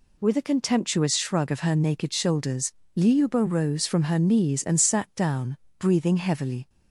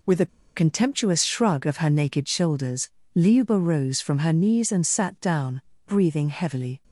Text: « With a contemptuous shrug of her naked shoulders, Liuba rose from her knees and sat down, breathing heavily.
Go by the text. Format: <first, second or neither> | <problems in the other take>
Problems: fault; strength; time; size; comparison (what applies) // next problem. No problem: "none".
first | pauses between "a" and "contemptuous"; slight; at 0.2 s; 0.29 s long